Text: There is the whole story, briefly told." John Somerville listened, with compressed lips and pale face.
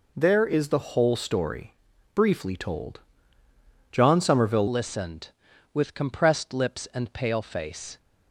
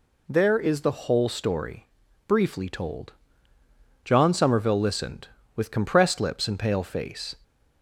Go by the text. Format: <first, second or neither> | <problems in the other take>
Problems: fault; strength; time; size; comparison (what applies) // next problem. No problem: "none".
second | changes voice at "listened"; from 4.6 s on; 3.3 s long